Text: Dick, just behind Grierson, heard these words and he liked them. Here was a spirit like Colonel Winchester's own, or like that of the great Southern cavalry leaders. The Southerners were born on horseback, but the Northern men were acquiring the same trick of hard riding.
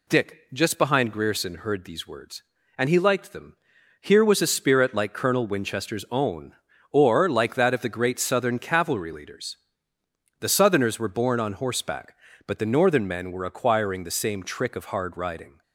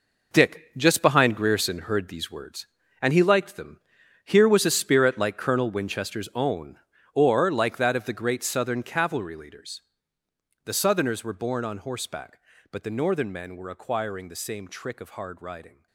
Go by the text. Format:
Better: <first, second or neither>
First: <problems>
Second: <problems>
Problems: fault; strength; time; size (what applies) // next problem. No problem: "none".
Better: first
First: none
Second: gets quieter; strong; throughout; 10.5 dB